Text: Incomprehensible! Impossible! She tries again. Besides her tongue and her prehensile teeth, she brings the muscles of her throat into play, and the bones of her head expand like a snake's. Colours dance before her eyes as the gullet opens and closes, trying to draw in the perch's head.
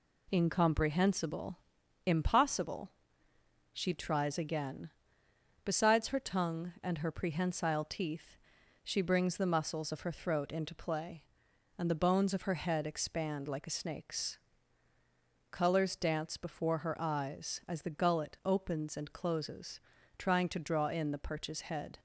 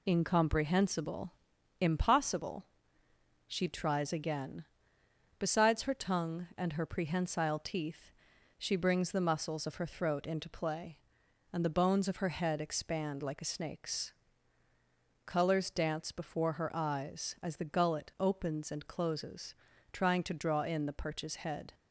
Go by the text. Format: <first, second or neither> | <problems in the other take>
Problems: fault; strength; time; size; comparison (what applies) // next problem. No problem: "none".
first | loses the start of "Incomprehensible"; at 0.0 s; 35 ms